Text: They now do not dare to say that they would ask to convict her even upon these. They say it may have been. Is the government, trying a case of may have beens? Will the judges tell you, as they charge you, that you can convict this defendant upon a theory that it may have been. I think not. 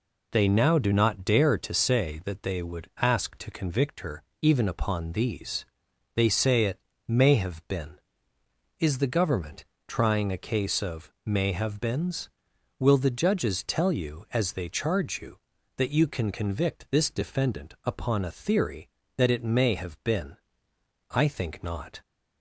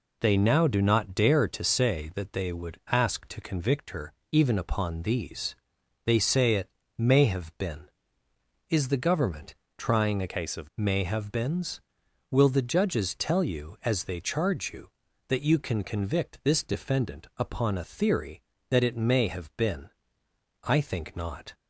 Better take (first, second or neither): first